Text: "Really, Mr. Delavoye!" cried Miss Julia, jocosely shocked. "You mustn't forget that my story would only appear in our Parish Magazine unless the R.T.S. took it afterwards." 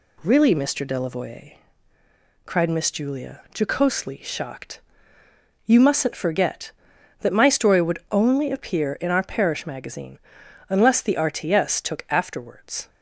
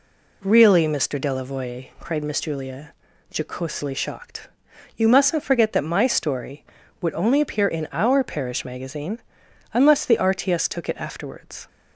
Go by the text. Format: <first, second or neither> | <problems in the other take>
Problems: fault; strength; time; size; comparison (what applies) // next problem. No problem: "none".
second | pauses between "Magazine" and "unless"; noticeable; at 10.1 s; 0.50 s long; noticeable in the second // skips "it"; at 12.0 s